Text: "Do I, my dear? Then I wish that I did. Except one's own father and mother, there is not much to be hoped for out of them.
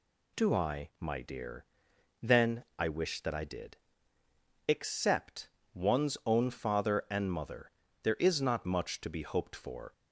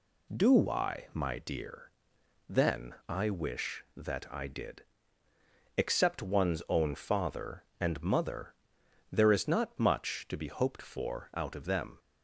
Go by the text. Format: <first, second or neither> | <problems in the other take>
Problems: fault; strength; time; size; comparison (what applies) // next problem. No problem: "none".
second | pauses between "Except" and "one's"; slight; at 5.4 s; 0.28 s long // stops before "out of them"; at 9.9 s